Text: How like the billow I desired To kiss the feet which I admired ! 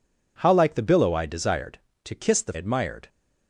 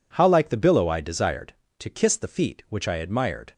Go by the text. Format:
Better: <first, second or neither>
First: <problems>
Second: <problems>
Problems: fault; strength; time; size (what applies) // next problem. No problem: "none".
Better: second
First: skips "feet which I"; at 2.5 s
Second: none